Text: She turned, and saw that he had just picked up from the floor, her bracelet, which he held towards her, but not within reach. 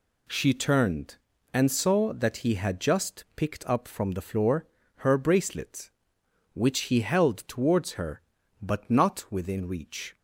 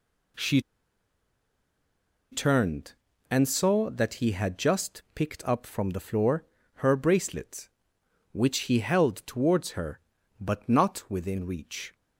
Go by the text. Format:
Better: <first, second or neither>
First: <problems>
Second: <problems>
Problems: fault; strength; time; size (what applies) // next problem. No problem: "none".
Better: first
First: none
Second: pauses between "She" and "turned"; strong; at 0.5 s; 1.7 s long